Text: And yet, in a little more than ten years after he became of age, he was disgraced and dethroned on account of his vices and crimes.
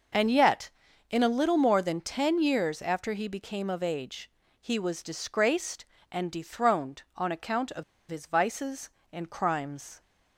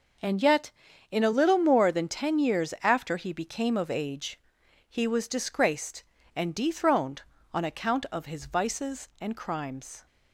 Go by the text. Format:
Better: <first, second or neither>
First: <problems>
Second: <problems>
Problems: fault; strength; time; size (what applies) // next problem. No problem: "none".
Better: second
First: pauses between "of" and "his"; slight; at 7.8 s; 0.26 s long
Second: none